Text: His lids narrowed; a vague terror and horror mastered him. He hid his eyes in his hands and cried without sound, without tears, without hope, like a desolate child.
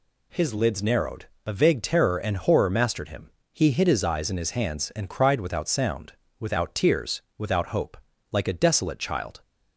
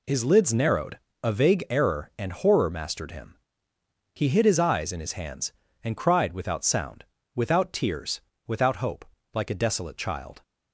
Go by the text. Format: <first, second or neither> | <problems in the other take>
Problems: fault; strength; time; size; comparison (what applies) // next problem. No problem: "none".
first | says "error" for "terror"; at 1.6 s